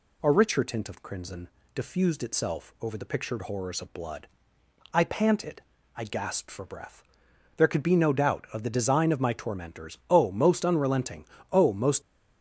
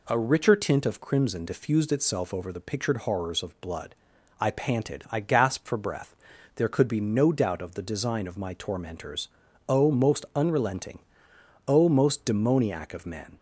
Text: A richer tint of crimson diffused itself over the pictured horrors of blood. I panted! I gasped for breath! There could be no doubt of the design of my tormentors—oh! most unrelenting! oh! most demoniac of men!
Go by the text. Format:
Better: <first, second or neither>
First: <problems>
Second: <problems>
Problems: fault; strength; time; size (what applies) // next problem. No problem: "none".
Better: second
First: pauses between "crimson" and "diffused"; slight; at 1.4 s; 0.26 s long // stops before "demoniac of men"; at 12.0 s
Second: none